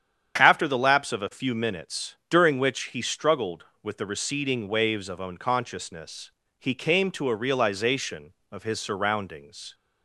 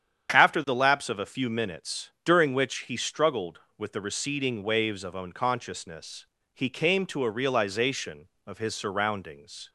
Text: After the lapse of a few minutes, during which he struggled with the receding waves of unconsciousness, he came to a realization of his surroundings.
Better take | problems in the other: neither | starts louder than the rest; strong; the same in both

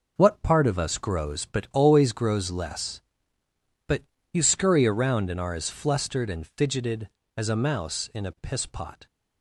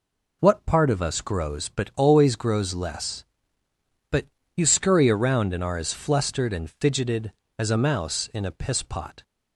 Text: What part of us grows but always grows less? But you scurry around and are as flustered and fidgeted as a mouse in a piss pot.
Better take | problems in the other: second | gets quieter; throughout; 7 dB // pauses between "But" and "you"; slight; at 4.0 s; 0.32 s long; slight in the second

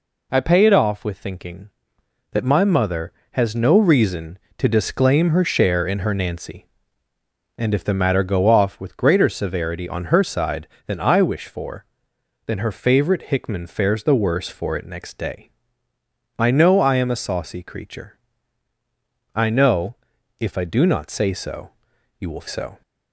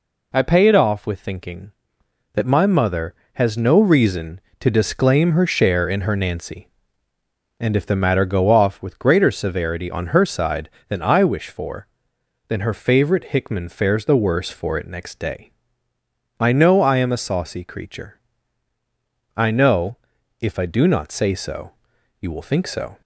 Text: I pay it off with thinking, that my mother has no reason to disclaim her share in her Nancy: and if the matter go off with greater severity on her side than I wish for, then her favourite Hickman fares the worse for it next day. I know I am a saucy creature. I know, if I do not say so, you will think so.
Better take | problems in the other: second | skips "think"; at 22.4 s

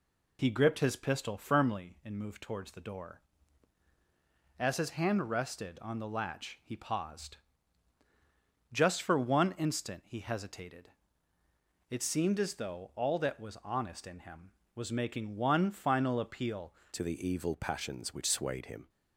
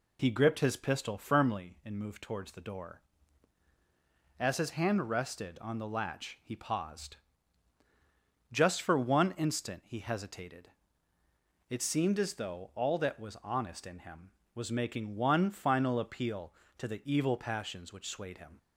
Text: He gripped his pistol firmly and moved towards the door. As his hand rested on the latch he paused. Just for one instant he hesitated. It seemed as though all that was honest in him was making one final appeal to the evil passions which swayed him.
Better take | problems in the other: second | changes voice at "to"; from 16.9 s on; 1.9 s long

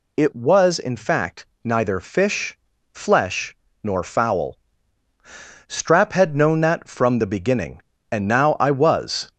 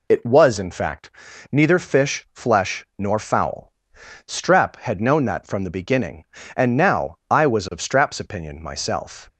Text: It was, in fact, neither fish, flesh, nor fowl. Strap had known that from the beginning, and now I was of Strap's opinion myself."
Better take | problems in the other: second | stops before "of Strap's opinion myself"; at 9.3 s

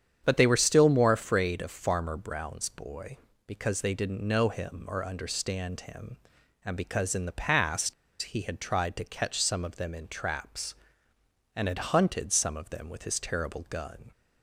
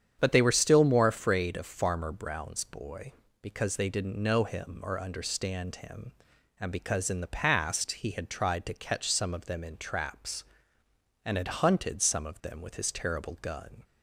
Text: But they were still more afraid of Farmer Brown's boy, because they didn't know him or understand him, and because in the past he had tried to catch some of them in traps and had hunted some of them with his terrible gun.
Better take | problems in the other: second | starts louder than the rest; strong; until 1.2 s; 8.5 dB; strong in the second // pauses between "past" and "he"; slight; at 7.9 s; 0.28 s long

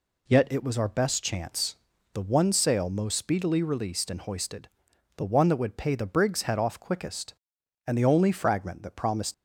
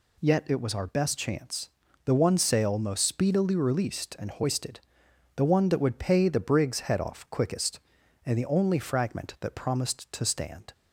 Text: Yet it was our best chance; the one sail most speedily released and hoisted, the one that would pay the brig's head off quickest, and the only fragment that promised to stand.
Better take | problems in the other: second | stops before "to stand"; at 9.3 s

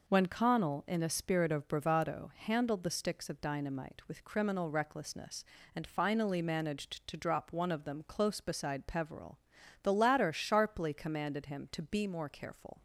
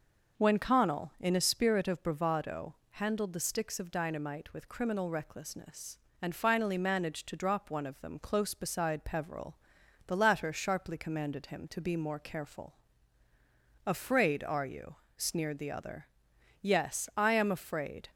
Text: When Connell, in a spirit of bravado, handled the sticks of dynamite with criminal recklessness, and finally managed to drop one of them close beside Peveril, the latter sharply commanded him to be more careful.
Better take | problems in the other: first | goes on to say "Afraid are you sneered the other Yes I am afraid"; strong; from 13.8 s on; 4.2 s long

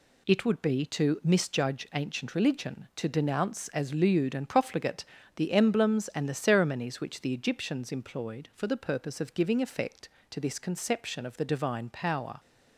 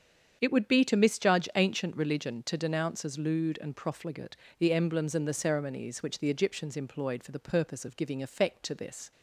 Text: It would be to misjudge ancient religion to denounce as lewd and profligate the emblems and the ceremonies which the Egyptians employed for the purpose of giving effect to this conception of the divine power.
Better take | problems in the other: first | starts louder than the rest; strong; until 1.4 s; 7.5 dB // pauses between "profligate" and "the"; slight; at 4.3 s; 0.24 s long; slight in the first // stops before "conception of the divine power"; at 9.1 s

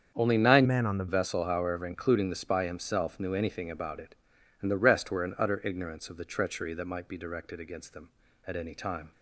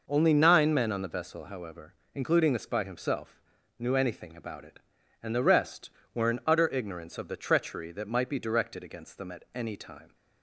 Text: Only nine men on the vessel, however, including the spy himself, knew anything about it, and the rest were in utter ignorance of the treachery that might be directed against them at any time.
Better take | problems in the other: second | starts louder than the rest; strong; until 1.1 s; 7.5 dB // changes voice from "men" to "the"; from 0.6 to 1.0 s; 0.4 s long

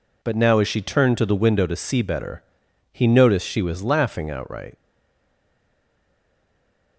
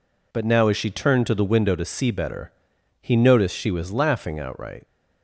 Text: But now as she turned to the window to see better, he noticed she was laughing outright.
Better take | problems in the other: second | stays silent after the last word; from 4.7 s on; 2.2 s long

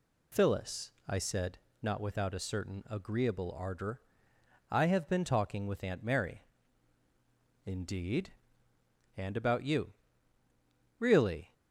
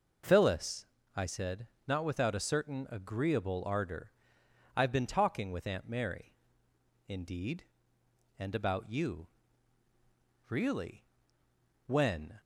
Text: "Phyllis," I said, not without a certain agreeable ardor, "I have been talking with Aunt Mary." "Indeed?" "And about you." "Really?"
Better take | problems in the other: first | goes on to say "When"; from 11.8 s on; 0.56 s long

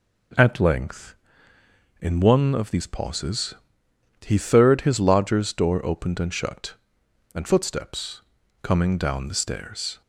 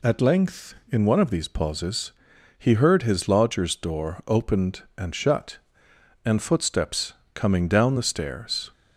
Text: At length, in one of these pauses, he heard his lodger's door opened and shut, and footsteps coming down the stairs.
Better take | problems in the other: second | says "third" for "heard"; at 4.3 s // pauses between "footsteps" and "coming"; at 8.2 s; 0.41 s long; slight in the second

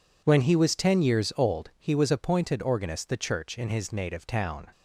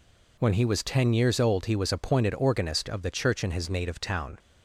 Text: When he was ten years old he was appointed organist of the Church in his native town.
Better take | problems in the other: second | skips "of"; at 3.0 s

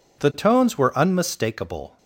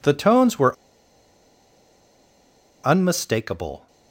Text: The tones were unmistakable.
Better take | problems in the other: first | pauses between "were" and "unmistakable"; strong; at 0.7 s; 2.0 s long

